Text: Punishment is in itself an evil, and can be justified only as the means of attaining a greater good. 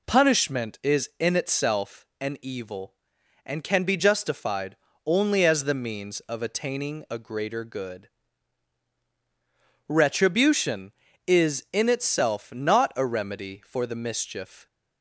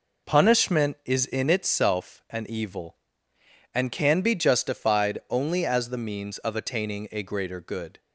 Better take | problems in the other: second | pauses between "justified" and "only"; slight; at 4.7 s; 0.30 s long // goes on to say "Retribution is in itself not a remedy for the mischief"; strong; from 9.8 s on; 4.7 s long

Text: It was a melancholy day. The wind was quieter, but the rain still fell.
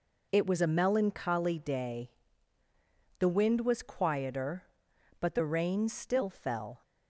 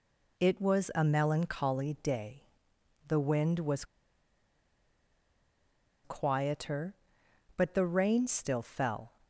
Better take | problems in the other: first | pauses between "was" and "quieter"; strong; at 3.8 s; 2.1 s long

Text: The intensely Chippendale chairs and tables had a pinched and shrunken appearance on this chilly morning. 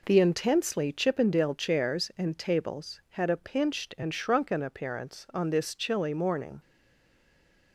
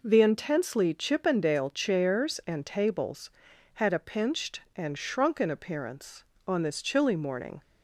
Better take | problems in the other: second | stays silent after the last word; from 6.6 s on; 1.1 s long

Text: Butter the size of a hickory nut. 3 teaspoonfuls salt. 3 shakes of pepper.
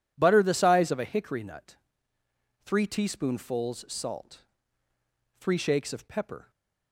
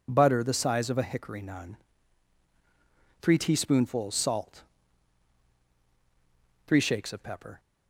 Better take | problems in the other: first | says "nun" for "nut"; at 1.4 s

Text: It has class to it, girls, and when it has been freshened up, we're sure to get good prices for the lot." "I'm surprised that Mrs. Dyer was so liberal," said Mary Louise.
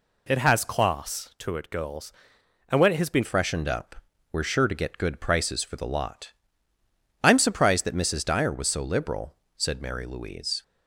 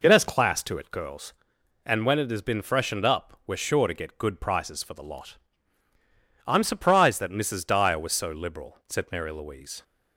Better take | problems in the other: second | changes voice at "freshened"; from 3.2 s on; 7.4 s long

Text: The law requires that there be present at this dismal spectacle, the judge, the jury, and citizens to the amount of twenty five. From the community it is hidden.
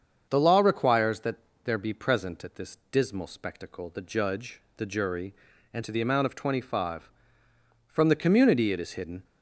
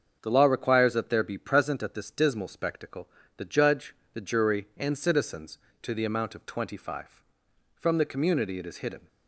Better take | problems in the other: second | starts louder than the rest; until 1.3 s; 7 dB; also in the second // pauses between "that" and "there"; slight; at 1.3 s; 0.28 s long // skips "citizens"; at 5.8 s

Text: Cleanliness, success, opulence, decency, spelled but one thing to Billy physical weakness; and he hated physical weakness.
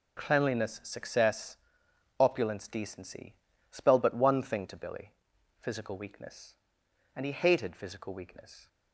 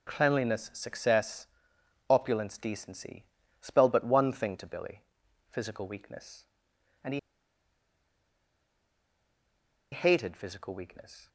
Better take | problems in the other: first | pauses between "Billy" and "physical"; noticeable; at 5.0 s; 0.48 s long; noticeable in the first // pauses between "he" and "hated"; strong; at 7.1 s; 2.7 s long

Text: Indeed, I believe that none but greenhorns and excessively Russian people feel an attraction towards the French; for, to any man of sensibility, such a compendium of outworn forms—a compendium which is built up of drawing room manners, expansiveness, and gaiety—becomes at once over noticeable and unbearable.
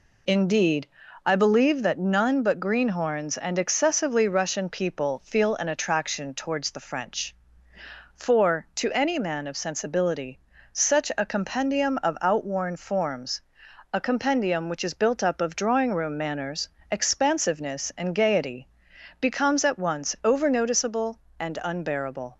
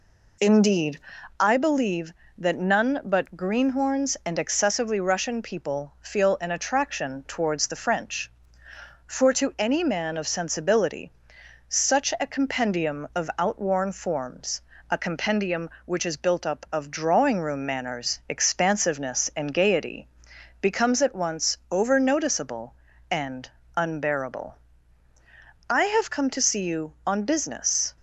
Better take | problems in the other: first | pauses between "and" and "unbearable"; slight; at 23.4 s; 0.26 s long // goes on to say "I have come to see you on business"; strong; from 25.6 s on; 2.2 s long

